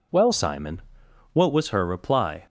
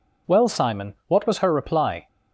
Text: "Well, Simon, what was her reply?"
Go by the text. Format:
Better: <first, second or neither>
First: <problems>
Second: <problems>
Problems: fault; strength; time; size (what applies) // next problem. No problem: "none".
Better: second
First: changes voice at "Simon"; from 0.3 s on; 2.1 s long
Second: none